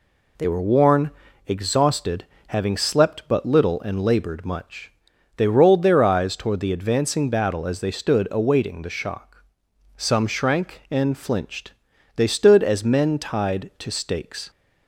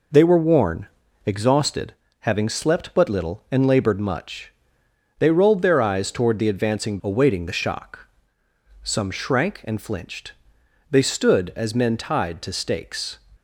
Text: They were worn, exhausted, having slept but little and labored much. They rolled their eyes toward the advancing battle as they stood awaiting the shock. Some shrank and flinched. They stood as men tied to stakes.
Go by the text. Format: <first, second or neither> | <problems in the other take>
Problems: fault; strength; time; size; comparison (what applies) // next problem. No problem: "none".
first | skips "battle as they stood"; at 6.9 s